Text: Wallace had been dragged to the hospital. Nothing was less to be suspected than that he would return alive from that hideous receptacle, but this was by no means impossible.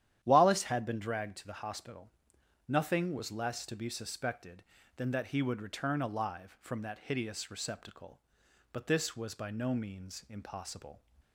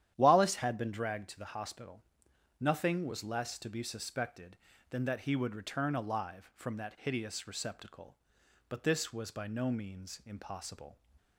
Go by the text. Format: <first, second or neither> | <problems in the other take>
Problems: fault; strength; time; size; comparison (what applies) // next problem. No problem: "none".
neither | starts louder than the rest; strong; the same in both